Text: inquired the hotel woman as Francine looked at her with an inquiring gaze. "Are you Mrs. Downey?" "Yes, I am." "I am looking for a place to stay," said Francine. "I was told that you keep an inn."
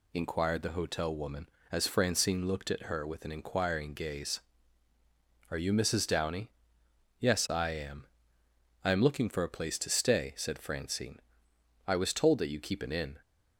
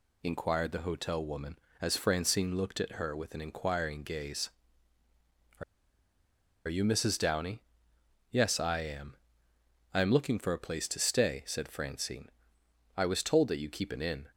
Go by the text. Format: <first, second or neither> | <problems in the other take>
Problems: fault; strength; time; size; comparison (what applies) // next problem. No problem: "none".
first | pauses between "Are" and "you"; at 5.6 s; 1.0 s long